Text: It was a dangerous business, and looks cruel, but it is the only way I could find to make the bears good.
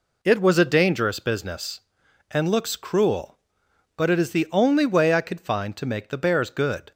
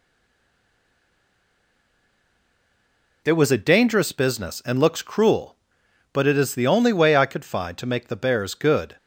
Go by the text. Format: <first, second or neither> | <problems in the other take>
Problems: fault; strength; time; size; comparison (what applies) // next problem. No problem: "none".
first | stays silent before the first word; strong; until 3.2 s; 3.2 s long